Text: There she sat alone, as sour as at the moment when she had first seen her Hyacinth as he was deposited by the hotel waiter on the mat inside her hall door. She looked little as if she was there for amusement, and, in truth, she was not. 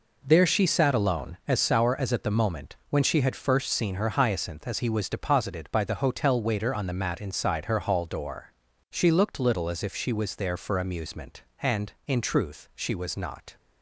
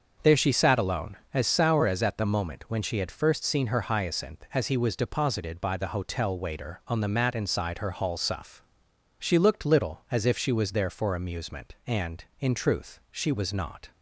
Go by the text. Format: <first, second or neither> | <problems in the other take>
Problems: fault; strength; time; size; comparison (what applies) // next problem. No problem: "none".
first | starts louder than the rest; until 1.4 s; 6.5 dB // says "suff" for "door"; at 8.1 s